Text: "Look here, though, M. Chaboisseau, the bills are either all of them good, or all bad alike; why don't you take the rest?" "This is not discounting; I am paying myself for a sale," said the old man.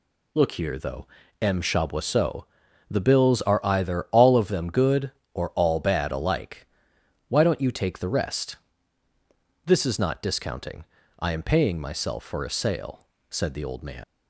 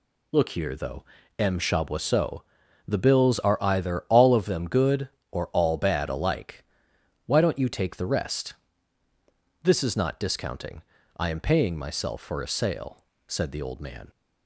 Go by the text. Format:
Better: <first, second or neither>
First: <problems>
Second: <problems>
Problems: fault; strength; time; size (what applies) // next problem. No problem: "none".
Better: second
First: leaves "man" unfinished; at 14.0 s; 85 ms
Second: none